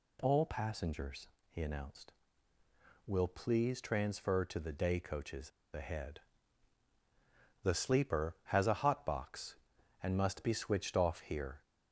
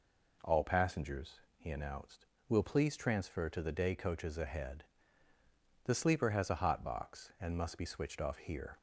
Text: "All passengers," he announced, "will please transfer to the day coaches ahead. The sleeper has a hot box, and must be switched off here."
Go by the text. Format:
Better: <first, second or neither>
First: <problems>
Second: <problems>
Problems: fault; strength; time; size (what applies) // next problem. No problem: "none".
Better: second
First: pauses between "coaches" and "ahead"; slight; at 5.5 s; 0.22 s long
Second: none